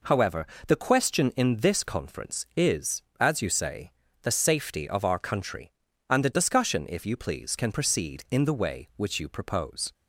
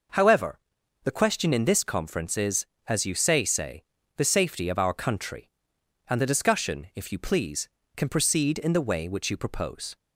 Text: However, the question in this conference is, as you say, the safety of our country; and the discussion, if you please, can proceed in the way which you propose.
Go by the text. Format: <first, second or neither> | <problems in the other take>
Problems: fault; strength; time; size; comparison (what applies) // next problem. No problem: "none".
first | says "say" twice; at 3.4 s